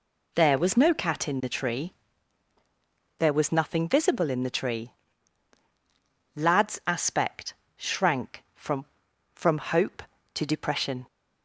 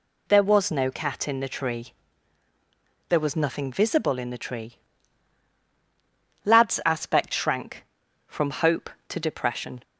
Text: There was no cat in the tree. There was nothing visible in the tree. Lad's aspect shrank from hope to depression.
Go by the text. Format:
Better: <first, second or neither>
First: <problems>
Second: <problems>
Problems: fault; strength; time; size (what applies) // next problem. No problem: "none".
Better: second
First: pauses between "aspect" and "shrank"; slight; at 7.5 s; 0.22 s long // says "from" twice; at 9.3 s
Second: none